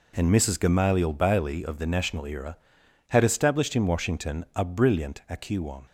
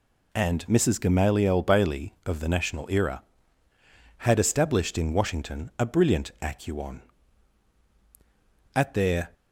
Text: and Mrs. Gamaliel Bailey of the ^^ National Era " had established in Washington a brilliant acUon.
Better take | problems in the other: first | goes on to say "At their"; from 8.7 s on; 0.58 s long

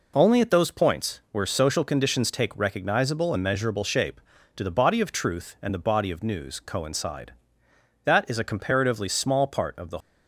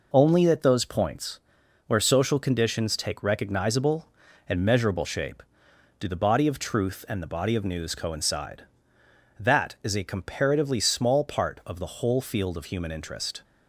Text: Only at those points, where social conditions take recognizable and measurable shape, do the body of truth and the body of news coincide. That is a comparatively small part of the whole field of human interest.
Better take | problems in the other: second | stops before "whole field of human interest"; at 9.9 s

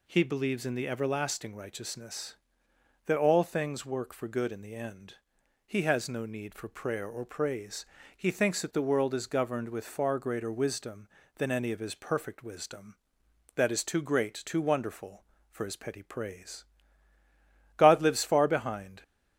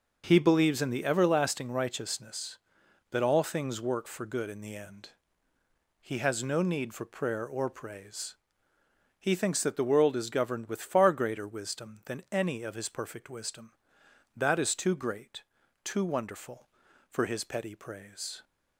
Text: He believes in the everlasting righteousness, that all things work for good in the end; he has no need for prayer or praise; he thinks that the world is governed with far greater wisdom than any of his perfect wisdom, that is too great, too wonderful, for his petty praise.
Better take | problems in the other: second | goes on to say "God lives far behind"; noticeable; from 17.7 s on; 1.2 s long

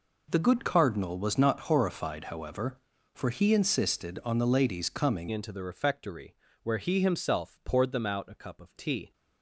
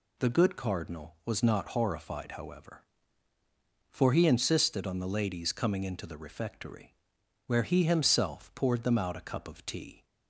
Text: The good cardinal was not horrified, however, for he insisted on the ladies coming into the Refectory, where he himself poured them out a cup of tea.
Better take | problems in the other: second | changes voice at "into"; from 5.3 s on; 3.8 s long

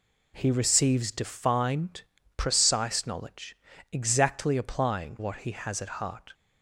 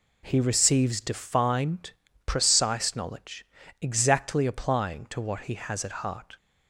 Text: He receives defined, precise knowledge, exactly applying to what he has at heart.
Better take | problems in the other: second | skips "to"; at 5.1 s

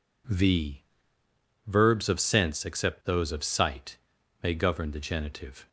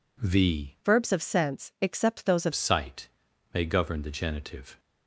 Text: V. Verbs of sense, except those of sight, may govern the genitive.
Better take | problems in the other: first | changes voice from "Verbs" to "of"; from 0.8 to 2.5 s; 1.7 s long

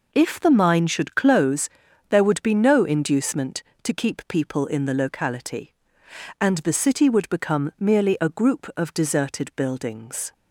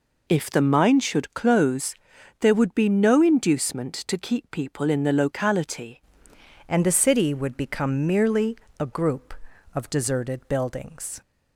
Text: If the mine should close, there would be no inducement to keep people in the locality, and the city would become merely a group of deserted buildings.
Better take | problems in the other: first | changes voice at "and"; from 6.6 s on; 4.6 s long // pauses between "merely" and "a"; slight; at 8.5 s; 0.24 s long

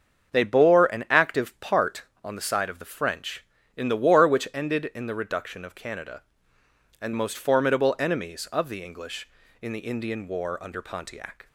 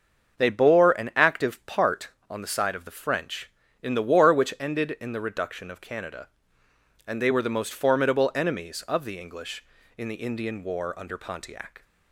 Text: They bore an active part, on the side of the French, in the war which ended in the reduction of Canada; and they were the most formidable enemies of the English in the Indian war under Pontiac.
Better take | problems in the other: second | starts louder than the rest; until 1.3 s; 7 dB; also in the second // skips "they were the"; at 7.1 s

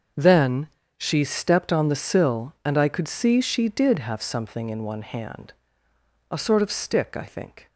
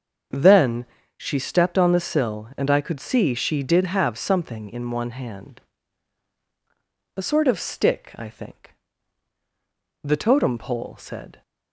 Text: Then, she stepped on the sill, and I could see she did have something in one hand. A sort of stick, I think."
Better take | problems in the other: first | starts louder than the rest; until 1.6 s; 7 dB; also in the first // goes on to say "The Totem Pole said"; from 10.0 s on; 1.3 s long

